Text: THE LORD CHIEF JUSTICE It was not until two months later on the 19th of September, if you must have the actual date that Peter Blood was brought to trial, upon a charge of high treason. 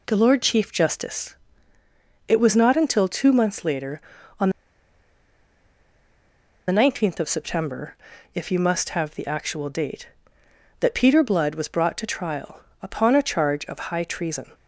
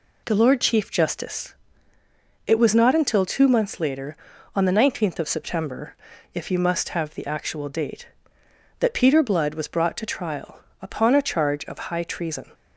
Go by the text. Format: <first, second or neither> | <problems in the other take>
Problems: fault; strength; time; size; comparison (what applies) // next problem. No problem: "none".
second | pauses between "JUSTICE" and "It"; noticeable; at 1.3 s; 0.94 s long; noticeable in the second // pauses between "on" and "the"; strong; at 4.5 s; 2.1 s long